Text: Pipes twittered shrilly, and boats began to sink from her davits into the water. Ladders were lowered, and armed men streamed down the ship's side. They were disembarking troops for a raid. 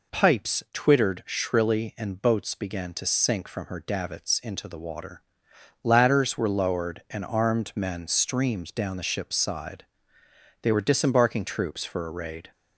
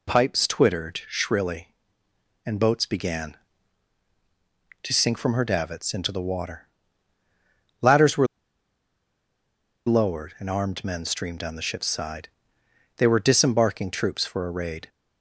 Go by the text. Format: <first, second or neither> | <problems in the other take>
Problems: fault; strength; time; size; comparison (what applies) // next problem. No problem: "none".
first | pauses between "were" and "lowered"; strong; at 8.2 s; 1.5 s long